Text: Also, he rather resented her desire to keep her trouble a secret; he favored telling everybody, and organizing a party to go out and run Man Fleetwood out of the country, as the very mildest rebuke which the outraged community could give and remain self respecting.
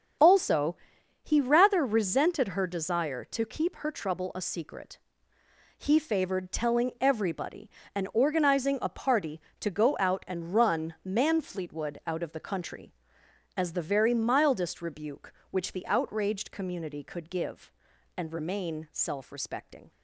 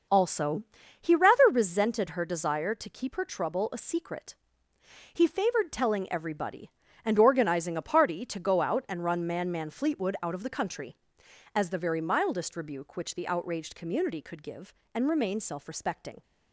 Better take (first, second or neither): first